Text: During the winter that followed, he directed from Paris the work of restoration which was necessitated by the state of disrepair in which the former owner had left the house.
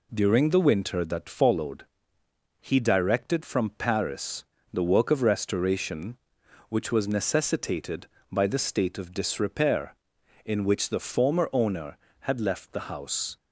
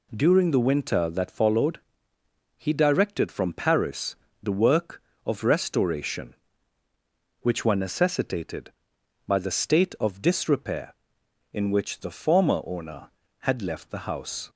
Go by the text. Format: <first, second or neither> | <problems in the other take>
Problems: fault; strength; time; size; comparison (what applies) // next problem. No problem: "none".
first | pauses between "Paris" and "the"; slight; at 4.1 s; 0.26 s long; slight in the first // says "were" for "was"; at 7.6 s